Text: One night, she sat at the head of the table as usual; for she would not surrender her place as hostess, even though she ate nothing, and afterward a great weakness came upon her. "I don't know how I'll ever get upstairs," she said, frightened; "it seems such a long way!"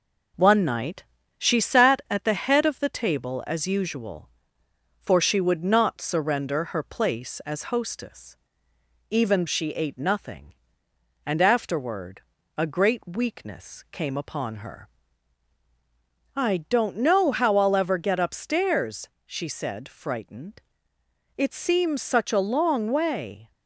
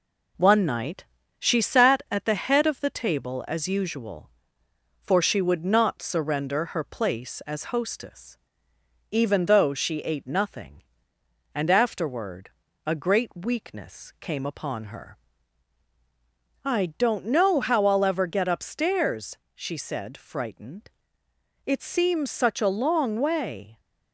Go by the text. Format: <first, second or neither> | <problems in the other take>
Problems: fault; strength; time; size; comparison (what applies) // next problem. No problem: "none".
second | skips "though"; at 9.4 s // pauses between "afterward" and "a"; slight; at 12.2 s; 0.36 s long; slight in the second